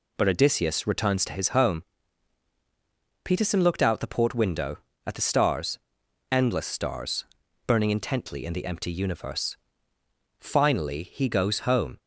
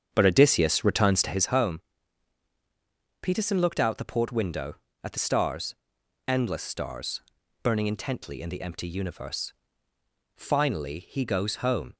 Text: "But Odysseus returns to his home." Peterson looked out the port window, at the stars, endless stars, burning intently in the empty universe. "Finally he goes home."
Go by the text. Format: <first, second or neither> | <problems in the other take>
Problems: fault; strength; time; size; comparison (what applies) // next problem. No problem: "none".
first | starts louder than the rest; strong; until 1.6 s; 7.5 dB